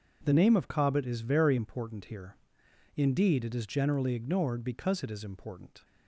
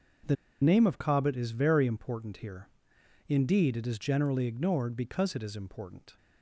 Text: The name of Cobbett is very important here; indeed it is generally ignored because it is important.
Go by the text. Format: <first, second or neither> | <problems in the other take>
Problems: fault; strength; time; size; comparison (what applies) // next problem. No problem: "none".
first | starts louder than the rest; until 1.5 s; 6.5 dB // pauses between "The" and "name"; slight; at 0.3 s; 0.27 s long